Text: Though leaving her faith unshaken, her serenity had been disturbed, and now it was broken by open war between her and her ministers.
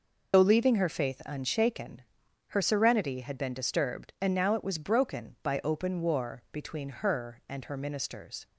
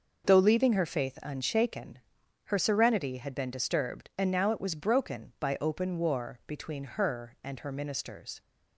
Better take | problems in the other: second | loses the start of "Though"; at 0.3 s; 65 ms

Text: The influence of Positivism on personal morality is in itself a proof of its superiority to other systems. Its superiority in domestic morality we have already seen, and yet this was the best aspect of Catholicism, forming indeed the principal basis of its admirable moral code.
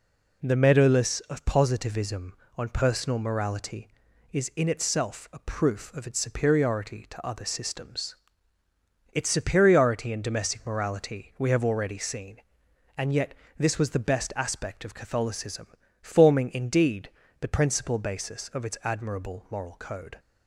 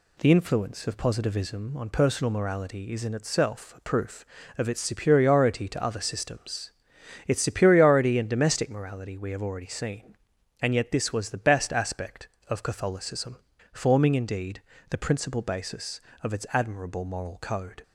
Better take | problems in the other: second | says "meadowless" for "influence"; at 0.5 s // pauses between "yet" and "this"; slight; at 13.3 s; 0.24 s long // pauses between "indeed" and "the"; slight; at 17.0 s; 0.32 s long; slight in the second

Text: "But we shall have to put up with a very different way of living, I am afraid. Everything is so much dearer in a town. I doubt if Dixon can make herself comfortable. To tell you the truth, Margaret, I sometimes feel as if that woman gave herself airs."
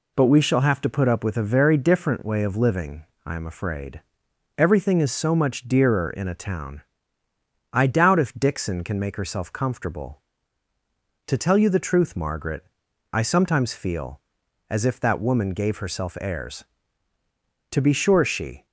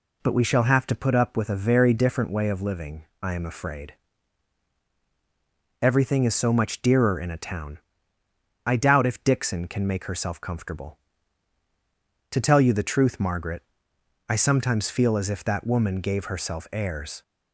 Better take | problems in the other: second | goes on to say "To be sure she"; noticeable; from 17.7 s on; 0.94 s long

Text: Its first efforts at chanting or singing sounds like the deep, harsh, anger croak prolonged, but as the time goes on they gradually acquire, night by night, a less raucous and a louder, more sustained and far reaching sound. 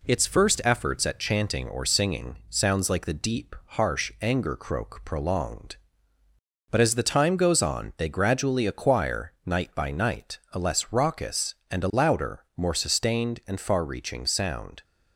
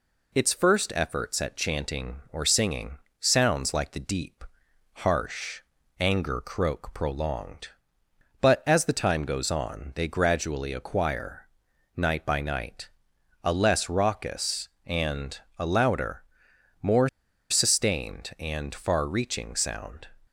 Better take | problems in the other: first | pauses between "singing" and "sounds"; slight; at 2.9 s; 0.28 s long // pauses between "and" and "a"; slight; at 15.4 s; 0.18 s long // pauses between "more" and "sustained"; at 17.0 s; 0.42 s long

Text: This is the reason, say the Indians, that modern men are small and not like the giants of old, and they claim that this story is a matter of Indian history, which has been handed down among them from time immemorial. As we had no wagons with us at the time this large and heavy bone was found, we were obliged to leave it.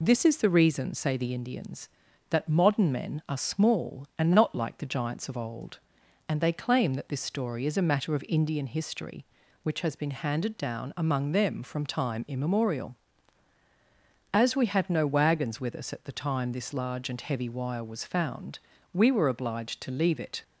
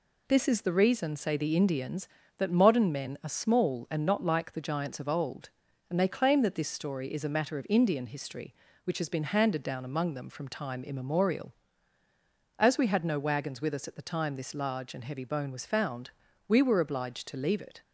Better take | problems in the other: second | says "wire" for "bone"; at 17.4 s

